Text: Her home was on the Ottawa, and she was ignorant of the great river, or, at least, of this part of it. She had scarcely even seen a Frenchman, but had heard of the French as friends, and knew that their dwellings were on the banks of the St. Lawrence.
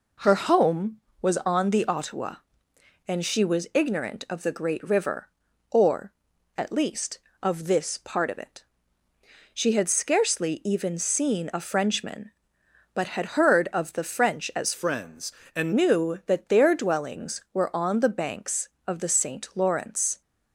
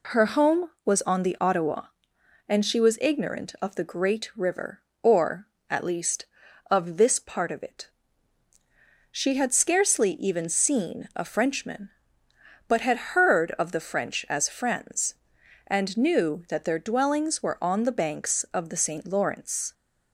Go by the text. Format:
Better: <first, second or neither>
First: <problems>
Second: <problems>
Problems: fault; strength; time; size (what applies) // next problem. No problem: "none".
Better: second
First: changes voice from "friends" to "and"; from 14.7 to 15.7 s; 1.0 s long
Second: none